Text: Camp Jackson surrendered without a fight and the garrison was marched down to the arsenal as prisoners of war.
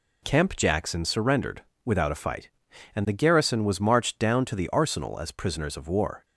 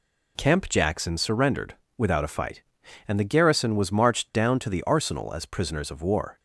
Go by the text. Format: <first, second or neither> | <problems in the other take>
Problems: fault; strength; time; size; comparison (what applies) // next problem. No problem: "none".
neither | pauses between "surrendered" and "without"; slight; the same in both